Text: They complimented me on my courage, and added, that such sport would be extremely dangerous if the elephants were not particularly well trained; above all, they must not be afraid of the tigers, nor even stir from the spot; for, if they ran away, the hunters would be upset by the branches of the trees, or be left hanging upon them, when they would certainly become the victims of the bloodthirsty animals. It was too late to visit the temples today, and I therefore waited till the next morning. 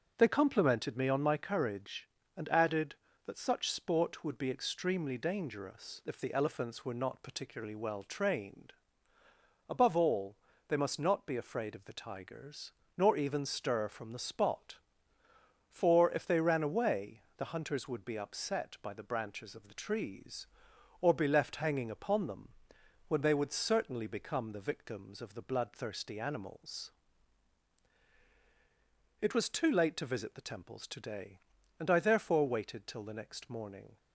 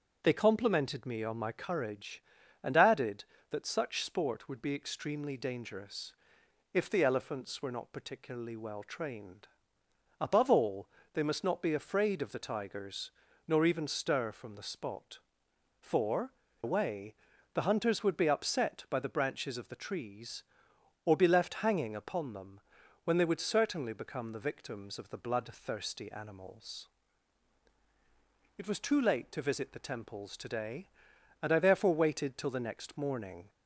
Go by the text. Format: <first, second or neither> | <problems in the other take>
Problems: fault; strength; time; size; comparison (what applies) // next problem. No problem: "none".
first | starts louder than the rest; until 1.2 s; 7 dB; strong in the first // pauses between "dangerous" and "if"; noticeable; at 6.1 s; 0.60 s long // skips "if they ran"; at 16.4 s